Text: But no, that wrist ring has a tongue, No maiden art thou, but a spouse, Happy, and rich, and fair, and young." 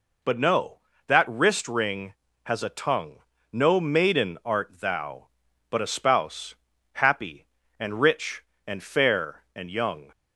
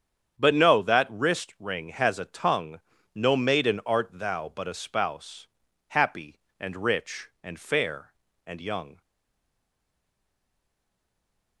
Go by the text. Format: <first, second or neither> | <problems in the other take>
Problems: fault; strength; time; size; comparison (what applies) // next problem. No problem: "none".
first | starts louder than the rest; strong; until 1.4 s; 8 dB // stays silent after the last word; strong; from 9.0 s on; 2.6 s long